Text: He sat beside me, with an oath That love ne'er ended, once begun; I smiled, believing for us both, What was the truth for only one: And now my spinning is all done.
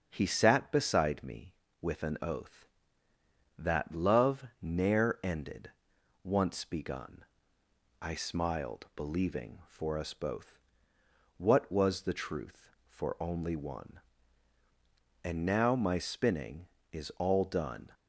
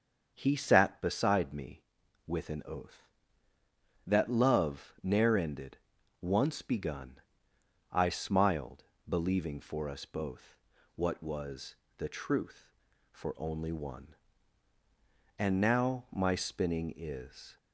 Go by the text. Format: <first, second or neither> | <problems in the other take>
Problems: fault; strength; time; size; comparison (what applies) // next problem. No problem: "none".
first | starts louder than the rest; until 1.3 s; 6.5 dB; also in the first // pauses between "was" and "the"; slight; at 11.7 s; 0.22 s long // stops before "all done"; at 17.5 s